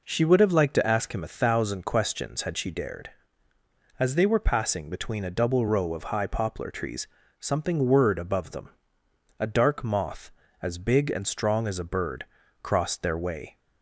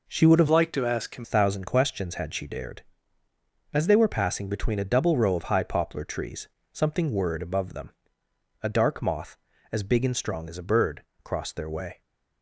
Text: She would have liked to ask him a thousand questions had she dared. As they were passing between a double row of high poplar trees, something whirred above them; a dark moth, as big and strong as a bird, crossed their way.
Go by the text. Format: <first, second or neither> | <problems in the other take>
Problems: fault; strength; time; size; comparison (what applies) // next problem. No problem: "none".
first | changes voice from "liked" to "him"; from 0.4 to 1.2 s; 0.8 s long